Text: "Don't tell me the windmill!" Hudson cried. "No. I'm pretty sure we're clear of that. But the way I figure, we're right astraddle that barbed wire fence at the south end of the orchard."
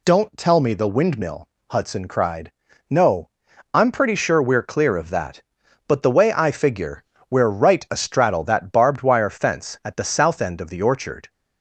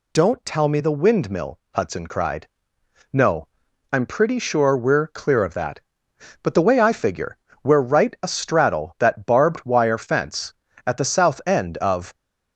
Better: first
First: none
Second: stops before "the orchard"; at 12.1 s

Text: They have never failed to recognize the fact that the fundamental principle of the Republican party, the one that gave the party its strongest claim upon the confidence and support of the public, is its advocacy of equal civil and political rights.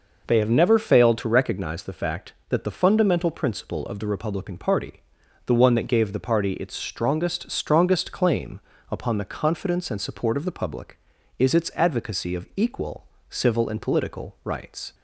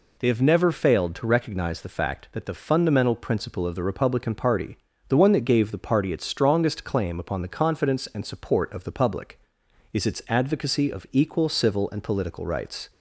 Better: second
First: says "strongest" twice; at 7.5 s // pauses between "claim" and "upon"; slight; at 8.6 s; 0.30 s long // pauses between "equal" and "civil"; slight; at 13.0 s; 0.22 s long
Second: none

